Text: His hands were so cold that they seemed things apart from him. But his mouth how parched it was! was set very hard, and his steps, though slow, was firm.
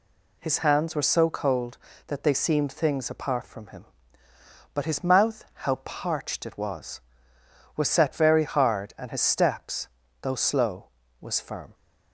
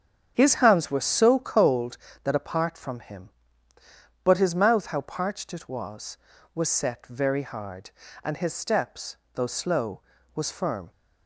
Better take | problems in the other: first | starts louder than the rest; strong; until 1.3 s; 7.5 dB // skips "they seemed things"; at 2.3 s

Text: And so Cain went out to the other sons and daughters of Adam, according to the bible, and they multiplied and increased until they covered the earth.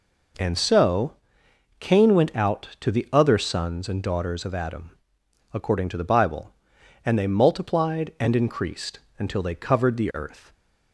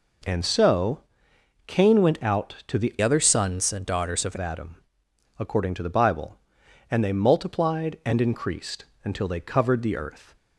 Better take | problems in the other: first | pauses between "so" and "Cain"; noticeable; at 1.0 s; 0.66 s long; noticeable in the first // changes voice from "other" to "of"; from 3.0 to 4.3 s; 1.3 s long // pauses between "increased" and "until"; slight; at 8.8 s; 0.18 s long; slight in the first

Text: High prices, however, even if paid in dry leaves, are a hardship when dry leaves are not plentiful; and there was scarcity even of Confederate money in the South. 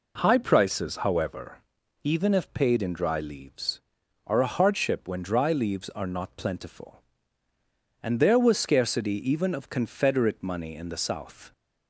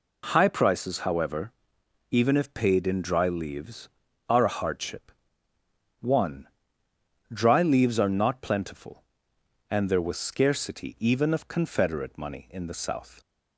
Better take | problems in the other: first | says "one" for "when"; at 6.0 s

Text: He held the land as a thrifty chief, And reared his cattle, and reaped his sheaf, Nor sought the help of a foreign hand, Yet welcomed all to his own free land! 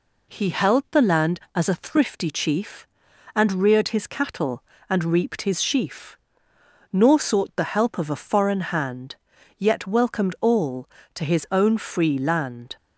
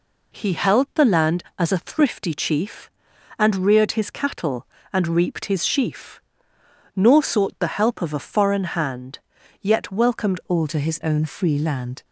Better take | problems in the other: first | changes voice at "all"; from 10.4 s on; 1.6 s long

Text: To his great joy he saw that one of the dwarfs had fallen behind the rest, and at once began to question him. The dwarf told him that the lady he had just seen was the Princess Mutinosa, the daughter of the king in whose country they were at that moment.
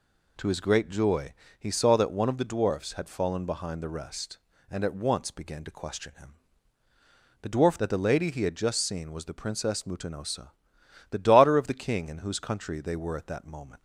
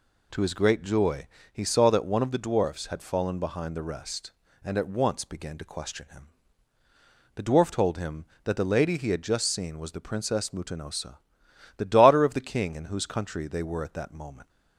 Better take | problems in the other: second | pauses between "joy" and "he"; slight; at 1.3 s; 0.26 s long; slight in the second // skips "told him"; at 7.7 s

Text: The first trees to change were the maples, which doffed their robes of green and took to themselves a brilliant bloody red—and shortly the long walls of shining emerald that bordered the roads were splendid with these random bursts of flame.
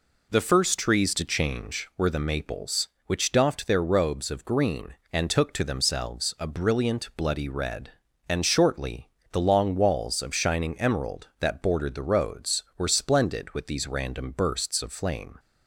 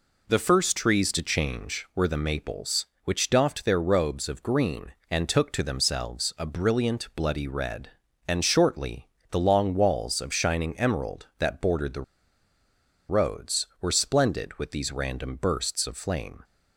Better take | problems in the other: first | pauses between "shortly" and "the"; slight; at 9.0 s; 0.22 s long; slight in the first // pauses between "the" and "roads"; at 12.0 s; 1.0 s long

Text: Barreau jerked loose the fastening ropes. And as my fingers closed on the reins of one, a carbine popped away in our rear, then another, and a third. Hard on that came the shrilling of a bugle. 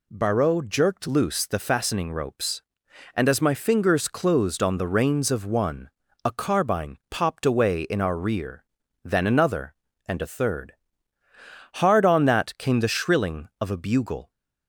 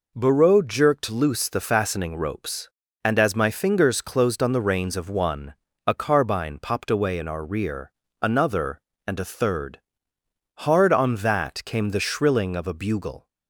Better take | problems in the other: first | skips "then"; at 8.0 s

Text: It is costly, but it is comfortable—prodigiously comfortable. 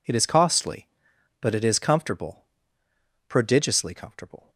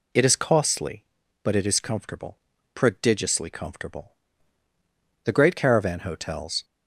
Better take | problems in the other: first | goes on to say "The great caravan hotels"; from 5.2 s on; 1.4 s long

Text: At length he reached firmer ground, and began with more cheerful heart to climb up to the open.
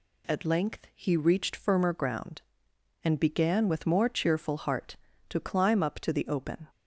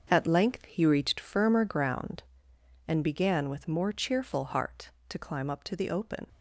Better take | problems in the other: first | gets quieter; strong; throughout; 9.5 dB

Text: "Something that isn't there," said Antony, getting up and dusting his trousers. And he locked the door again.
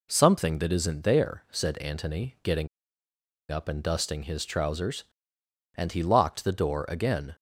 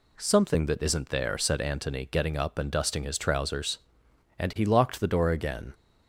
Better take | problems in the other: second | pauses between "getting" and "up"; noticeable; at 2.6 s; 0.83 s long

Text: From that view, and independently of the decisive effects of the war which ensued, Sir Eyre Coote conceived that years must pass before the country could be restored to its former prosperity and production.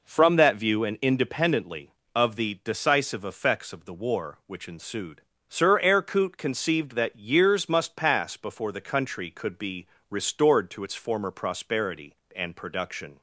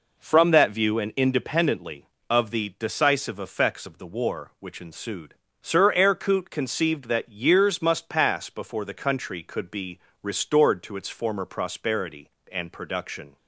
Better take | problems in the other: neither | pauses between "be" and "restored"; slight; the same in both

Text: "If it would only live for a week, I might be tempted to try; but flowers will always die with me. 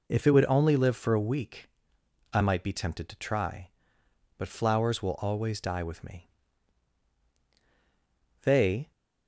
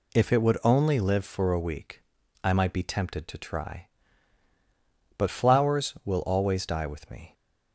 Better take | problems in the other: second | goes on to say "They"; slight; from 8.4 s on; 0.48 s long

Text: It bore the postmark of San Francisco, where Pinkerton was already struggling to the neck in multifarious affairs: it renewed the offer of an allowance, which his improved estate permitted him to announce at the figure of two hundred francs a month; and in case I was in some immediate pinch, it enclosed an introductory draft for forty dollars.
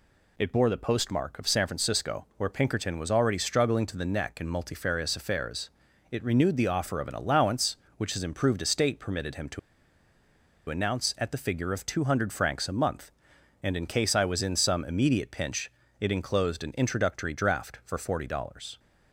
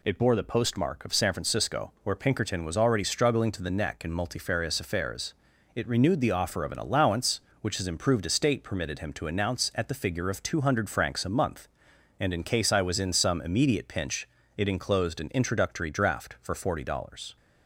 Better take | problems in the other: second | pauses between "to" and "announce"; at 9.5 s; 1.0 s long

